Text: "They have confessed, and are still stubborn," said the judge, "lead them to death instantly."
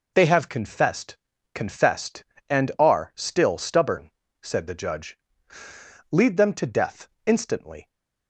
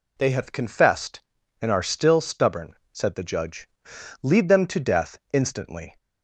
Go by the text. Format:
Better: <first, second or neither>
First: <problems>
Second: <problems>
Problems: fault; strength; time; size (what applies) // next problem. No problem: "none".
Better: second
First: says "confessed" twice; at 1.5 s // pauses between "death" and "instantly"; slight; at 7.0 s; 0.18 s long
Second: pauses between "death" and "instantly"; slight; at 5.1 s; 0.16 s long